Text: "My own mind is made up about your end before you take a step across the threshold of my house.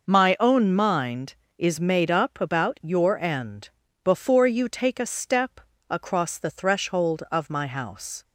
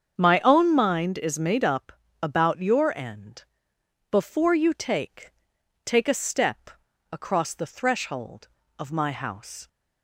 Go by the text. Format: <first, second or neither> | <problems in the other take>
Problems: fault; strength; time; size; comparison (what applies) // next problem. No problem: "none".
first | starts louder than the rest; strong; until 1.2 s; 7.5 dB // pauses between "up" and "about"; slight; at 1.9 s; 0.30 s long // pauses between "end" and "before"; noticeable; at 3.4 s; 0.66 s long; slight in the first // says "take" twice; at 5.8 s // pauses between "step" and "across"; at 6.6 s; 0.42 s long; slight in the first